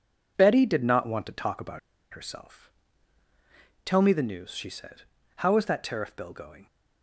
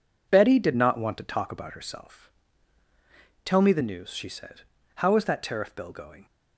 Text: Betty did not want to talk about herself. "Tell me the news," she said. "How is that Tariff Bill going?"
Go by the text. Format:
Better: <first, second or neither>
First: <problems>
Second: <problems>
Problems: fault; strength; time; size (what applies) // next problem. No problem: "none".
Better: second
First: pauses between "about" and "herself"; slight; at 1.7 s; 0.34 s long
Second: none